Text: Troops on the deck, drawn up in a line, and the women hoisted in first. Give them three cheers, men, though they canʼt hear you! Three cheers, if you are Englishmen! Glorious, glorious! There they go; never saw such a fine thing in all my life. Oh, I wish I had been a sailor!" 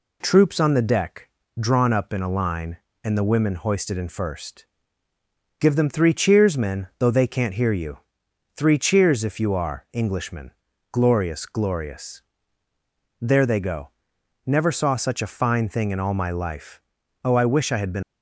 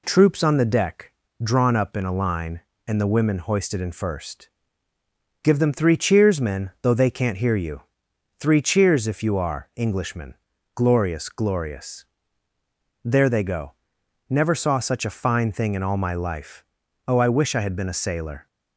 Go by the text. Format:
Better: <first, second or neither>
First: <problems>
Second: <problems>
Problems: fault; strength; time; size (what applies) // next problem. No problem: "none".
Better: second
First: stops before "a sailor"; at 18.0 s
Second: none